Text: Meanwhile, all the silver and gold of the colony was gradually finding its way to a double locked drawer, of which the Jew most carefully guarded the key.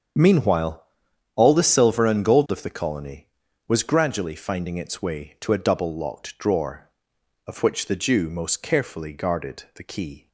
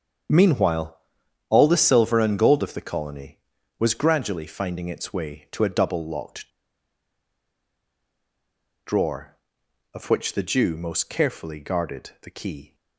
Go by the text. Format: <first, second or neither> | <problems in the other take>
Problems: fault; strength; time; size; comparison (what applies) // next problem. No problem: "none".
first | starts louder than the rest; strong; until 1.8 s; 7.5 dB; strong in the first // pauses between "locked" and "drawer"; strong; at 6.4 s; 2.3 s long